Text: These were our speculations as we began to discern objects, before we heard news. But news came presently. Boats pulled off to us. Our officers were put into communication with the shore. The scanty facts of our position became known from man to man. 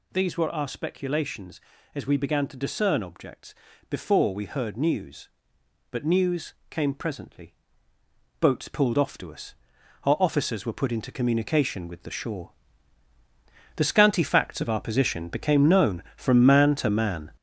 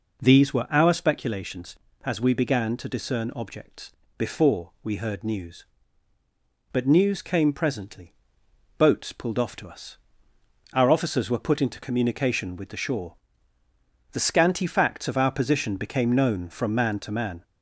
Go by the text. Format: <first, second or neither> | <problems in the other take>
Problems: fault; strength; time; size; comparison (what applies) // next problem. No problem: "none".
second | gets louder; throughout; 6 dB // pauses between "news" and "came"; slight; at 6.5 s; 0.16 s long